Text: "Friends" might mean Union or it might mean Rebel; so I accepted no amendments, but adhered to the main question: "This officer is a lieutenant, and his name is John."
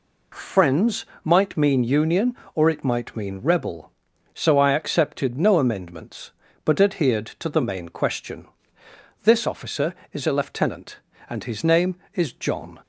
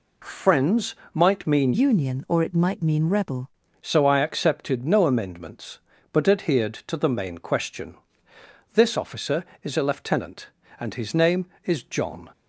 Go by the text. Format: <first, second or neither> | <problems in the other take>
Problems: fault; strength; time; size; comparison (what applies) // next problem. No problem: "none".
first | pauses between "Friends" and "might"; slight; at 0.9 s; 0.18 s long; slight in the first // changes voice from "Union" to "Rebel"; from 1.7 to 3.5 s; 1.8 s long